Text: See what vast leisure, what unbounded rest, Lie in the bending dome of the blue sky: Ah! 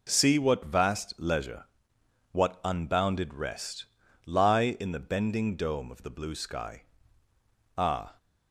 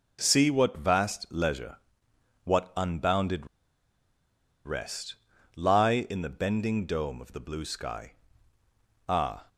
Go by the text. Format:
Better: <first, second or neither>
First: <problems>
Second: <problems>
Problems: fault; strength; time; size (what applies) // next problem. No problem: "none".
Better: first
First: none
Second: pauses between "unbounded" and "rest"; at 3.4 s; 1.1 s long